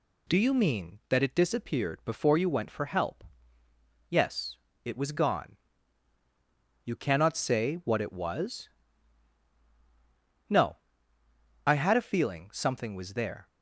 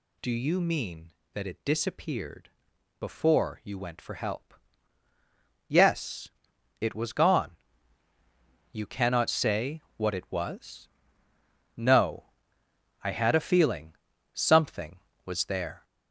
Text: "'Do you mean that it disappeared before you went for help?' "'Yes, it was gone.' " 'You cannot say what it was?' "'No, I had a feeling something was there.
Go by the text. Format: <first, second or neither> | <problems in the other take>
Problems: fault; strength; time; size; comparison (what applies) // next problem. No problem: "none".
first | gets louder; noticeable; throughout; 4.5 dB // pauses between "disappeared" and "before"; noticeable; at 2.4 s; 0.50 s long // pauses between "say" and "what"; slight; at 9.8 s; 0.16 s long // pauses between "feeling" and "something"; at 13.9 s; 0.42 s long